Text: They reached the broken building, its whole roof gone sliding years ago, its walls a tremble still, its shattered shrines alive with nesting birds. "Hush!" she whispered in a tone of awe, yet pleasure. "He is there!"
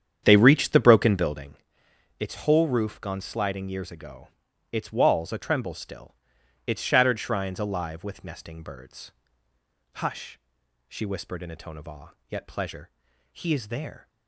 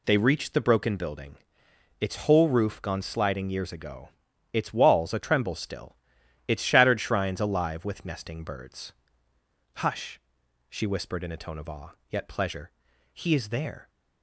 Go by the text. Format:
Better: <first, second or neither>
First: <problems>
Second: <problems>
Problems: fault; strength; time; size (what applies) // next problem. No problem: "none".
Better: second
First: starts louder than the rest; strong; until 1.6 s; 8.5 dB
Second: none